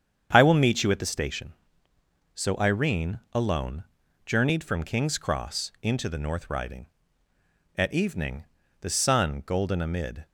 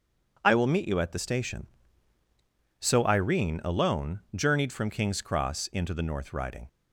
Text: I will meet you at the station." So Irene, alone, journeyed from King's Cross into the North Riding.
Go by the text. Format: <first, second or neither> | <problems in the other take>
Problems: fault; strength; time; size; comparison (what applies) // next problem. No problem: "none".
second | starts louder than the rest; strong; until 1.3 s; 7.5 dB // goes on to say "At evening the sun golden amid"; strong; from 7.7 s on; 2.5 s long